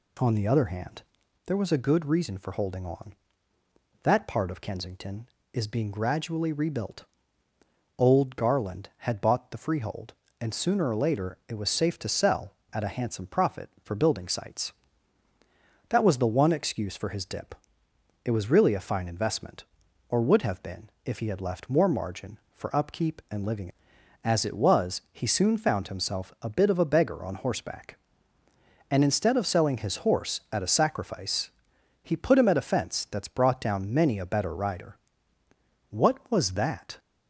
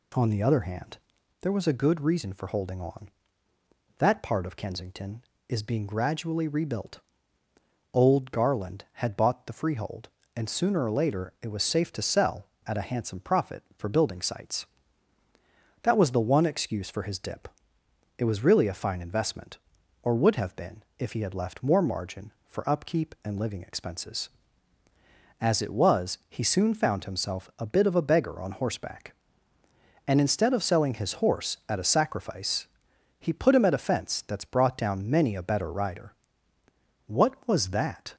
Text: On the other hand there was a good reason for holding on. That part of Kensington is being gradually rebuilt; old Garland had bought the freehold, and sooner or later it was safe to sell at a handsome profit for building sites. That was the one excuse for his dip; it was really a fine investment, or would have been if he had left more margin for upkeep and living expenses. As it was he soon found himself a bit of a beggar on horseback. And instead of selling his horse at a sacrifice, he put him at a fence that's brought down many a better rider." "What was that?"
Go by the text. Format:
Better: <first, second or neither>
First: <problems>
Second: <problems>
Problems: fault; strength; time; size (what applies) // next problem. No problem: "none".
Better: second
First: pauses between "hand" and "there"; at 1.0 s; 0.44 s long // pauses between "been" and "if"; slight; at 20.8 s; 0.16 s long // skips "expenses"; at 23.9 s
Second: pauses between "hand" and "there"; at 0.9 s; 0.44 s long // pauses between "been" and "if"; slight; at 20.8 s; 0.16 s long